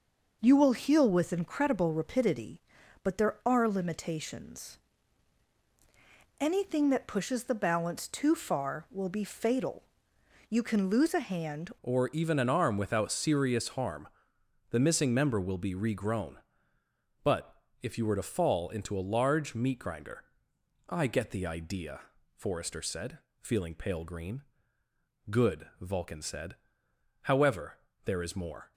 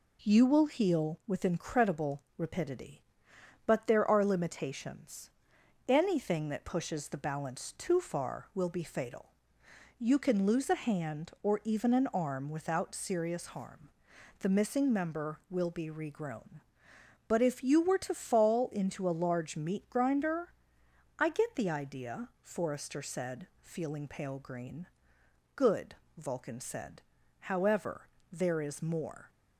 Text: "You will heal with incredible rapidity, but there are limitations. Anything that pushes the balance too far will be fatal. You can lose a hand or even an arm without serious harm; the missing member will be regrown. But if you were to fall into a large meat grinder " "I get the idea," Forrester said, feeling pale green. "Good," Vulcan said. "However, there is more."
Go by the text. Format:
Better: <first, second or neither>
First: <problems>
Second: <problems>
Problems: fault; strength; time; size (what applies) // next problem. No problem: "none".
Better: second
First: changes voice at "or"; from 11.8 s on; 16.9 s long // pauses between "But" and "if"; slight; at 17.6 s; 0.20 s long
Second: none